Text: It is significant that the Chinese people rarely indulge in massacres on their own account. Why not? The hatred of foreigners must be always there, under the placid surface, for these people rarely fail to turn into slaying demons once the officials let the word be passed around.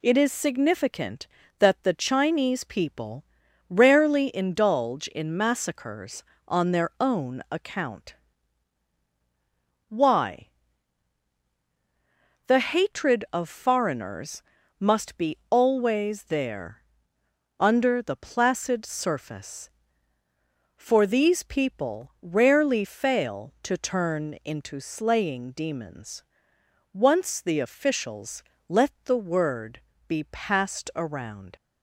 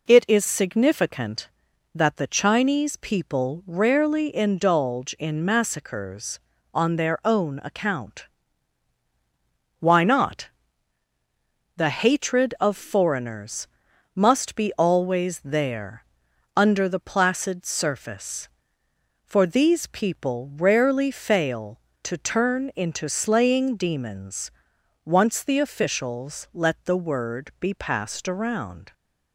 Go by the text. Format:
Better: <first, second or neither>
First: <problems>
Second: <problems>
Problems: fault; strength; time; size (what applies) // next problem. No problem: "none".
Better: second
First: pauses between "people" and "rarely"; noticeable; at 3.2 s; 0.46 s long // skips "not"; at 11.4 s // pauses between "foreigners" and "must"; at 14.4 s; 0.38 s long // pauses between "demons" and "once"; noticeable; at 26.2 s; 0.68 s long // pauses between "officials" and "let"; slight; at 28.4 s; 0.26 s long // pauses between "word" and "be"; slight; at 29.7 s; 0.28 s long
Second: pauses between "foreigners" and "must"; noticeable; at 13.6 s; 0.48 s long // pauses between "demons" and "once"; noticeable; at 24.5 s; 0.54 s long